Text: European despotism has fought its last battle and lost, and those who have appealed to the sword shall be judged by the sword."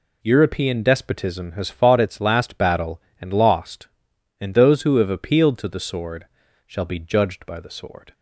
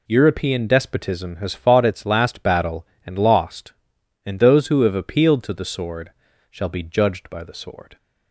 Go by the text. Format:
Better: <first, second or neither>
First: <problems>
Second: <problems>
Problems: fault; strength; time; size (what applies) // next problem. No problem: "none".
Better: neither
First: pauses between "sword" and "shall"; at 6.2 s; 0.42 s long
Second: pauses between "sword" and "shall"; at 6.1 s; 0.40 s long